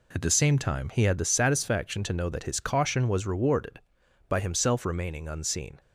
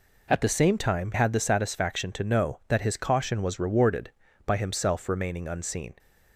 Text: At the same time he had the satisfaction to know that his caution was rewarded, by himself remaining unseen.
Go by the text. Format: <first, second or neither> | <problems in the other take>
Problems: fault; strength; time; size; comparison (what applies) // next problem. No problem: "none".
first | skips "he"; at 1.1 s